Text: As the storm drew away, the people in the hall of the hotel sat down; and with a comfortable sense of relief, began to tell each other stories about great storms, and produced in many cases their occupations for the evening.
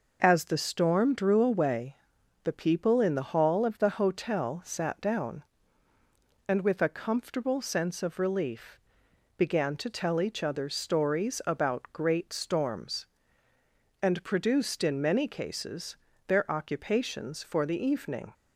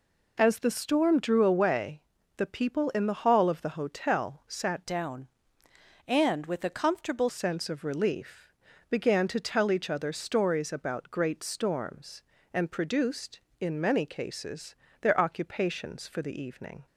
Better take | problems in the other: first | changes voice from "down" to "comfortable"; from 4.8 to 7.2 s; 2.4 s long // pauses between "cases" and "their"; slight; at 14.7 s; 0.28 s long; slight in the first

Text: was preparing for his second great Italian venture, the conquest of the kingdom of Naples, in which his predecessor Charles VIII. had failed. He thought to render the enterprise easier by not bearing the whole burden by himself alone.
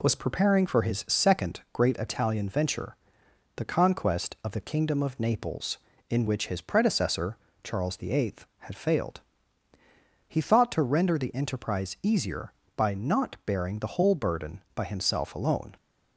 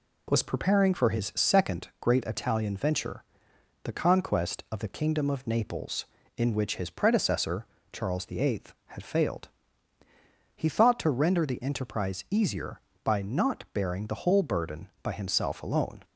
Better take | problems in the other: neither | pauses between "predecessor" and "Charles"; slight; the same in both

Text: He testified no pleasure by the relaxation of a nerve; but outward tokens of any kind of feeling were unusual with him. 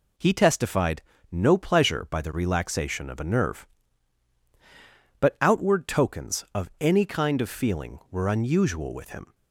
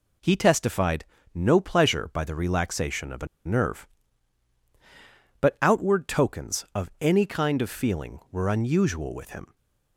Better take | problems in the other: first | pauses between "testified" and "no"; slight; at 1.0 s; 0.28 s long; slight in the first // pauses between "a" and "nerve"; slight; at 3.2 s; 0.18 s long // stays silent after the last word; slight; from 9.4 s on; 0.5 s long

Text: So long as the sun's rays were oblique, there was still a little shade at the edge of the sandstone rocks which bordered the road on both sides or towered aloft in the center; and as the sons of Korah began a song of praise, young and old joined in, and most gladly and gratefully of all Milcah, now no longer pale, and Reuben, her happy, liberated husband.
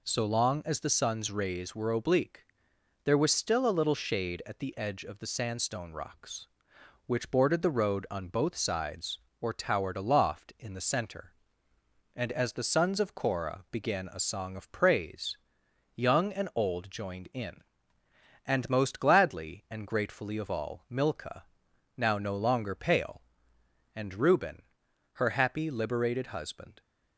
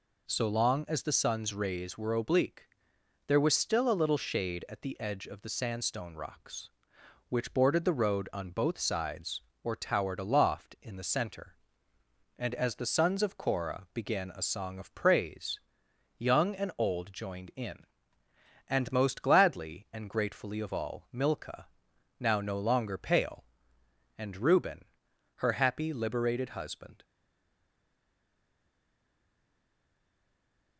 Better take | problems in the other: first | stays silent after the last word; strong; from 27.0 s on; 3.7 s long

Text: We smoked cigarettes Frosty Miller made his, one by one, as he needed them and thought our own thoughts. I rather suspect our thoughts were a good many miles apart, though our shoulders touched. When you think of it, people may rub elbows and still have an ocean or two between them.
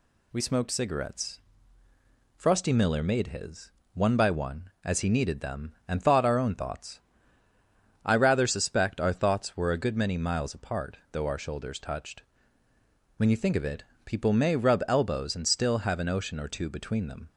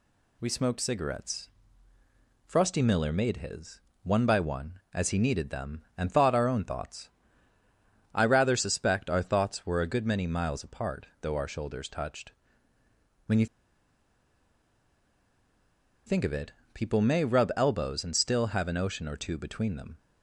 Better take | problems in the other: first | pauses between "cigarettes" and "Frosty"; noticeable; at 1.4 s; 0.94 s long; noticeable in the first // pauses between "you" and "think"; strong; at 13.4 s; 2.6 s long

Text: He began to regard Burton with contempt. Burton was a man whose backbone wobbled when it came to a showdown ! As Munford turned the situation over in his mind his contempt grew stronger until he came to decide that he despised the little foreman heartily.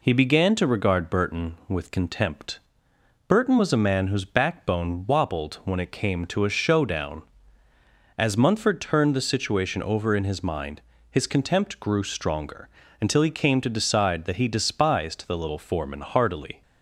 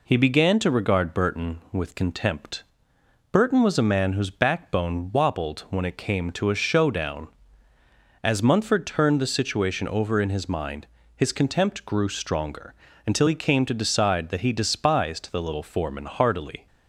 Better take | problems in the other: neither | pauses between "mind" and "his"; slight; the same in both // pauses between "stronger" and "until"; slight; the same in both

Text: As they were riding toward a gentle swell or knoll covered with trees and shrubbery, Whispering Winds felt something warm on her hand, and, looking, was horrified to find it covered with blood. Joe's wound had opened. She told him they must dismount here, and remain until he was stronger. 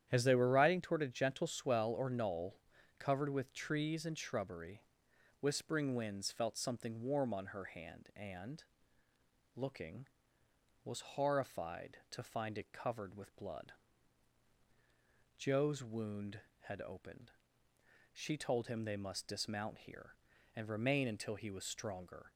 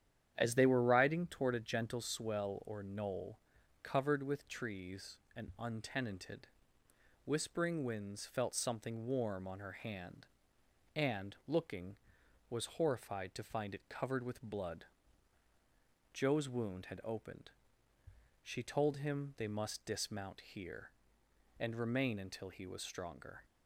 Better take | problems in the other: first | starts louder than the rest; strong; until 1.3 s; 9.5 dB; strong in the first // pauses between "knoll" and "covered"; at 3.3 s; 0.44 s long; also in the first // says "untenanted" for "shrubbery"; at 5.5 s

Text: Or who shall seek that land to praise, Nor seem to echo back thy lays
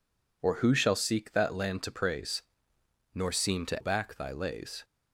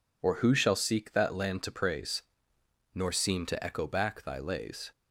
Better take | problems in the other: second | skips "echo"; at 3.8 s

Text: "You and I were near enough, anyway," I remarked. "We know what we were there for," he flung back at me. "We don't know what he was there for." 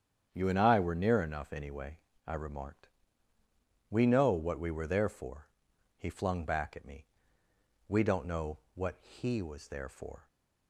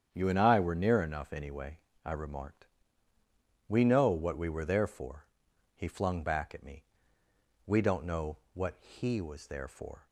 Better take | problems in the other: neither | starts louder than the rest; strong; the same in both // pauses between "know" and "what"; slight; the same in both

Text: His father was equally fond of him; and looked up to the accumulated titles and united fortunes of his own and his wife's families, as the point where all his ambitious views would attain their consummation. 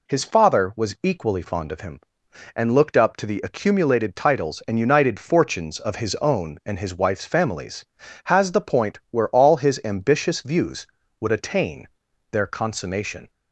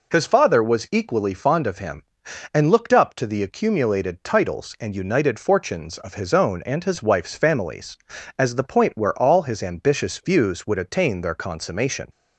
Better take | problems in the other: second | says "has" for "as"; at 8.2 s // pauses between "attain" and "their"; at 11.8 s; 0.42 s long

